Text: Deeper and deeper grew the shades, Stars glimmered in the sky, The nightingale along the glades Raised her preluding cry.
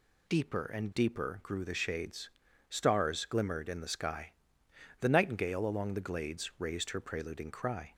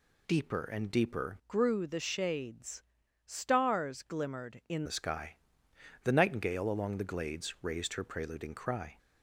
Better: first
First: none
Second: changes voice from "grew" to "in"; from 1.4 to 4.8 s; 3.4 s long

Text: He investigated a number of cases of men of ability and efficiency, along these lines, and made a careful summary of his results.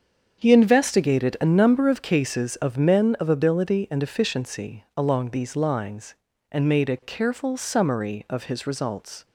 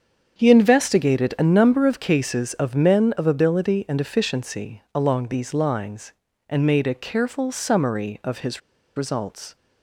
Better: first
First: starts louder than the rest; strong; until 1.4 s; 7 dB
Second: starts louder than the rest; strong; until 1.4 s; 7 dB // pauses between "his" and "results"; at 8.5 s; 0.36 s long

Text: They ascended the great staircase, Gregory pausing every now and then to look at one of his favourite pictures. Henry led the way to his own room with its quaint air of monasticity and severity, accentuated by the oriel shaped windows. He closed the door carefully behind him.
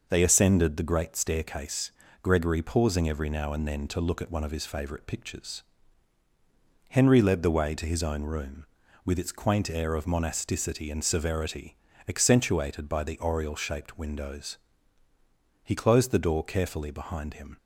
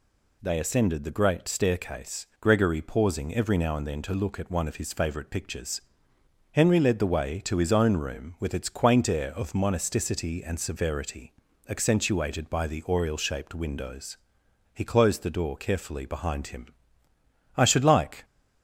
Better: first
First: none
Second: goes on to say "I should like"; noticeable; from 17.5 s on; 0.68 s long

